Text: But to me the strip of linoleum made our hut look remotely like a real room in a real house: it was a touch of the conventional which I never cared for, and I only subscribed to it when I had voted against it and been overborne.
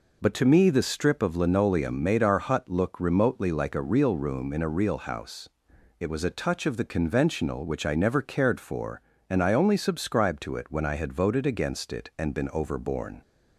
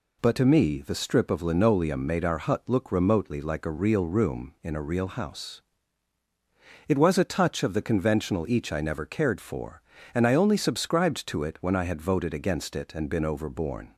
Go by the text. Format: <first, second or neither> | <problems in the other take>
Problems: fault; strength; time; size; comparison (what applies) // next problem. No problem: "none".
first | says "each" for "which"; at 8.4 s